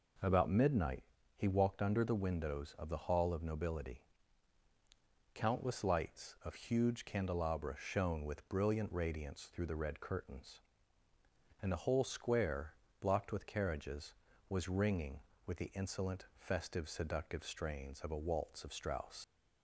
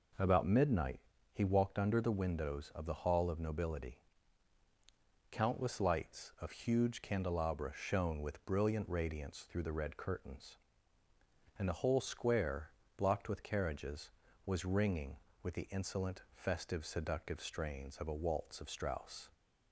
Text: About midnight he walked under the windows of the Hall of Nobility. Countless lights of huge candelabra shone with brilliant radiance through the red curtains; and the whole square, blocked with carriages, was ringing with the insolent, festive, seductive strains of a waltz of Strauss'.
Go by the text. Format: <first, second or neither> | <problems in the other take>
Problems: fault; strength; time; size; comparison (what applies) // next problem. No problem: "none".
second | pauses between "midnight" and "he"; slight; at 1.0 s; 0.32 s long; slight in the second // leaves "Strauss" unfinished; at 19.2 s; 120 ms